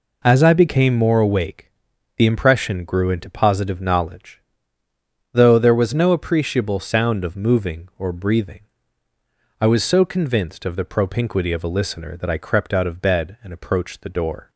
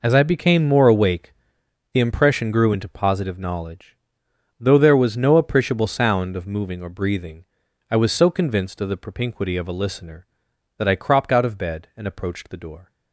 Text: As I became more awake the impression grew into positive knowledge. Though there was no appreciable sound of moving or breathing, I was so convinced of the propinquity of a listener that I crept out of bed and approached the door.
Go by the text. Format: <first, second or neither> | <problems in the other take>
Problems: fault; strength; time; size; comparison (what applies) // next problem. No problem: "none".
first | pauses between "awake" and "the"; noticeable; at 1.3 s; 0.60 s long; also in the first // says "cropped" for "crept"; at 10.9 s